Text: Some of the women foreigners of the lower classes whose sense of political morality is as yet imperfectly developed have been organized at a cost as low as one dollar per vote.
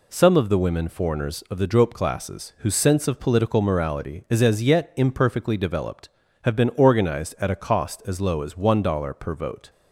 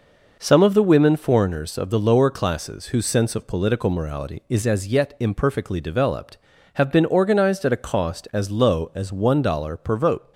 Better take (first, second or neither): second